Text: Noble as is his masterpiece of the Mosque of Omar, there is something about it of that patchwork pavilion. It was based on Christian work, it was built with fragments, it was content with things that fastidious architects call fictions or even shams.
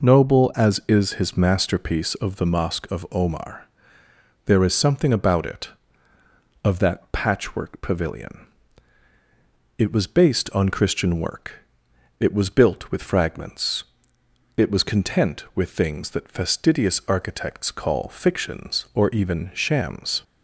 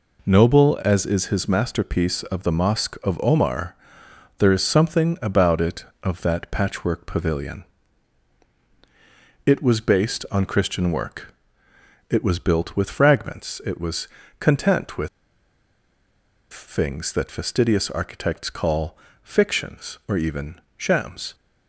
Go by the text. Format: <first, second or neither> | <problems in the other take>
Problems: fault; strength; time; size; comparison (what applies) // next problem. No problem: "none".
first | pauses between "was" and "content"; slight; at 14.0 s; 0.30 s long // pauses between "with" and "things"; strong; at 15.0 s; 1.4 s long // pauses between "call" and "fictions"; slight; at 18.9 s; 0.26 s long // pauses between "even" and "shams"; slight; at 20.6 s; 0.16 s long